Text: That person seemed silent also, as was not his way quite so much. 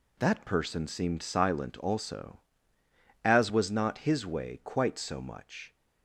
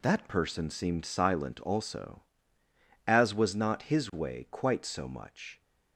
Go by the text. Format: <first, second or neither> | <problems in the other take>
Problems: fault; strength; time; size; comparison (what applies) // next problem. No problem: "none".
neither | none